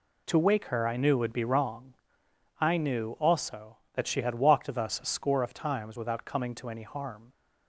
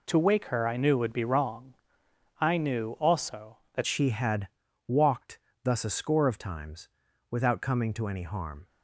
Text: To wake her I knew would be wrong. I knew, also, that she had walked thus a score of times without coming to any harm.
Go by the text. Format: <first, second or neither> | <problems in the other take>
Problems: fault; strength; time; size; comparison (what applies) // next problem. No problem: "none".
first | changes voice at "she"; from 3.8 s on; 4.8 s long // pauses between "had" and "walked"; at 4.4 s; 0.38 s long // pauses between "walked" and "thus"; slight; at 5.3 s; 0.24 s long // pauses between "times" and "without"; at 6.8 s; 0.40 s long